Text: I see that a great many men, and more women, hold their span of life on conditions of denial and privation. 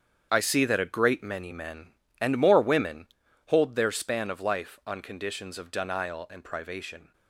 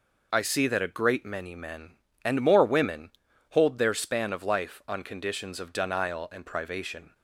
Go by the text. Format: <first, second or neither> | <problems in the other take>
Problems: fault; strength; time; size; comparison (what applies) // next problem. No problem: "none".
second | gets quieter; strong; throughout; 11.5 dB